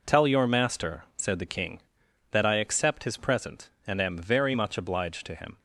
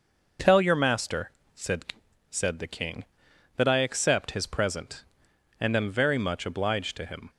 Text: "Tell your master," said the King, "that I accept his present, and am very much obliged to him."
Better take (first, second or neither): first